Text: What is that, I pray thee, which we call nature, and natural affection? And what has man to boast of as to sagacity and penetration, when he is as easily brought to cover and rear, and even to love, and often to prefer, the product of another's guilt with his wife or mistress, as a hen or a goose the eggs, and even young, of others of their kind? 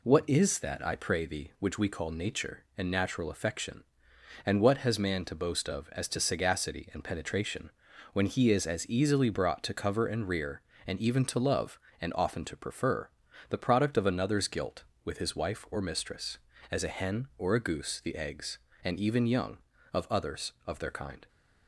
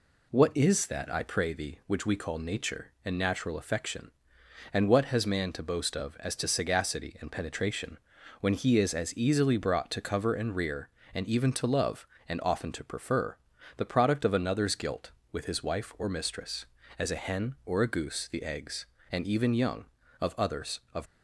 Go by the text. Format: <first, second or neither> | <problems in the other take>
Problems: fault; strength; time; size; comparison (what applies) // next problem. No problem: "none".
first | stops before "their kind"; at 21.0 s